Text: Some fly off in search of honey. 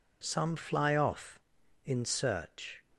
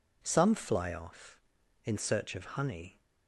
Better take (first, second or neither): second